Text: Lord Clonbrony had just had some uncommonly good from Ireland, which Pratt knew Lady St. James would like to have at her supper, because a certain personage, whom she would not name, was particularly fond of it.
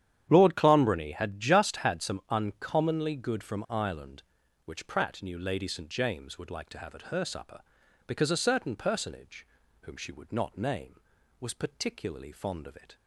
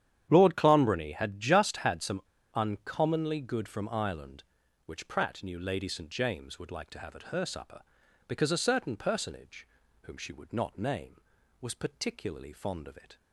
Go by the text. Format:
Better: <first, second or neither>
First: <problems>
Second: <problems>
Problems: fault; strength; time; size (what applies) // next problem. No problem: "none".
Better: first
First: starts louder than the rest; strong; until 1.3 s; 10 dB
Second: starts louder than the rest; strong; until 1.3 s; 10 dB // pauses between "some" and "uncommonly"; slight; at 2.2 s; 0.32 s long